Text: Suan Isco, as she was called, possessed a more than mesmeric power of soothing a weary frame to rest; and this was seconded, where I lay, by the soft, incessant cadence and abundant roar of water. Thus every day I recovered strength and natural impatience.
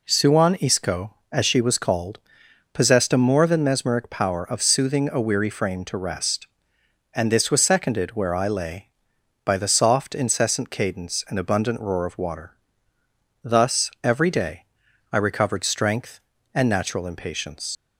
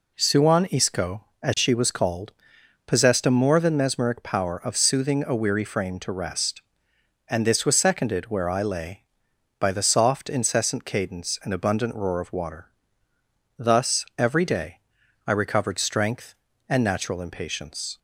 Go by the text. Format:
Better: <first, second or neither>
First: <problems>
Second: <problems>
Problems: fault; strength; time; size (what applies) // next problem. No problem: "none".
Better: second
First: pauses between "day" and "I"; noticeable; at 14.6 s; 0.48 s long // leaves "impatience" unfinished; at 17.7 s; 85 ms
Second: pauses between "day" and "I"; noticeable; at 14.7 s; 0.48 s long